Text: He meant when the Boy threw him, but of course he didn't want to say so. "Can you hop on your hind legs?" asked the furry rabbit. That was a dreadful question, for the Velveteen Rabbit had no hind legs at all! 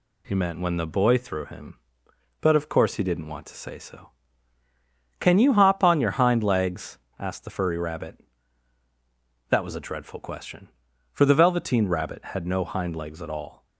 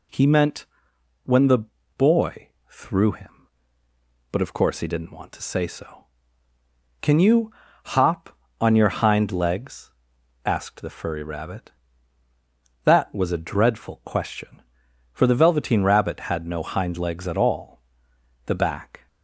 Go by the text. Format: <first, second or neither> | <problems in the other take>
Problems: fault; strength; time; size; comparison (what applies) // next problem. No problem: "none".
first | pauses between "meant" and "when"; noticeable; at 0.6 s; 0.58 s long // pauses between "the" and "Boy"; slight; at 1.5 s; 0.36 s long // pauses between "Boy" and "threw"; slight; at 2.4 s; 0.22 s long // pauses between "you" and "hop"; slight; at 7.5 s; 0.36 s long // goes on to say "The back"; noticeable; from 18.4 s on; 0.62 s long